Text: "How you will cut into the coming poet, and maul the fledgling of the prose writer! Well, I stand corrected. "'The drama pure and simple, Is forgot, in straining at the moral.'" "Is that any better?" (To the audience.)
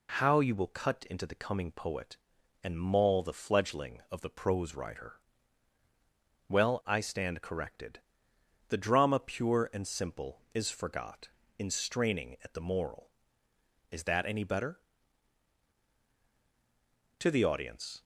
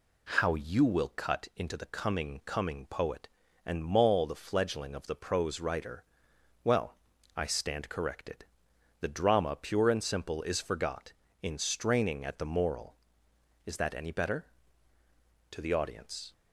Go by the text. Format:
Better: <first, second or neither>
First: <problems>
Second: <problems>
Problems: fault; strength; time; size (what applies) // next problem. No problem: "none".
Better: first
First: none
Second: says "coming" twice; at 2.4 s